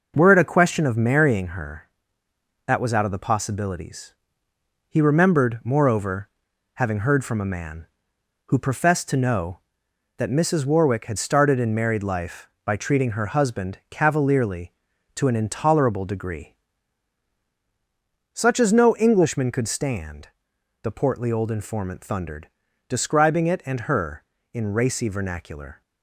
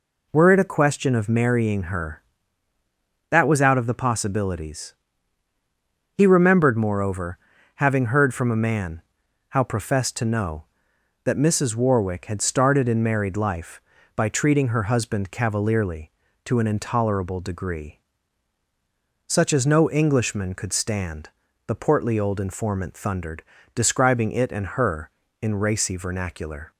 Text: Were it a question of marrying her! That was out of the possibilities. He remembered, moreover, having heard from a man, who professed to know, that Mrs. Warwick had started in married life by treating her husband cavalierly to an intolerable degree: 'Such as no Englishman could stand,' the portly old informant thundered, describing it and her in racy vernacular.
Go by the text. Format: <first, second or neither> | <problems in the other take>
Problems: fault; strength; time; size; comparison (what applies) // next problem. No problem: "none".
first | says "how" for "who"; at 9.5 s